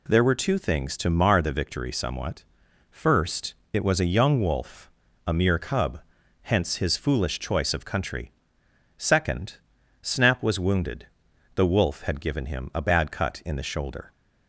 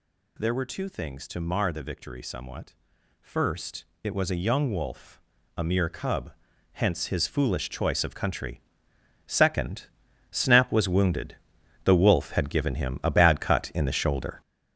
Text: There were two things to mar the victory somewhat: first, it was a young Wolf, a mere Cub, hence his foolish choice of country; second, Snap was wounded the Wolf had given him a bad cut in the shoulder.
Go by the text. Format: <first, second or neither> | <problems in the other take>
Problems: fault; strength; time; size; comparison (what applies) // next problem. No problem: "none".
first | gets louder; strong; throughout; 7.5 dB // pauses between "wounded" and "the"; noticeable; at 11.3 s; 0.48 s long; noticeable in the first